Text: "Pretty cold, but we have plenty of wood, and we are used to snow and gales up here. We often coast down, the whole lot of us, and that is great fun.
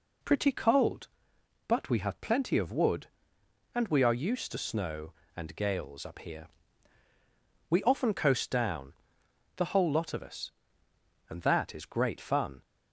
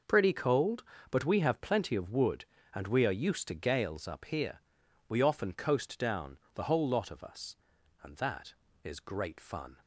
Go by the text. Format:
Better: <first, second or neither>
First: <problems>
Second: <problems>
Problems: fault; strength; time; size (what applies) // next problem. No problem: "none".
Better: first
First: none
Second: skips "snow and"; at 3.5 s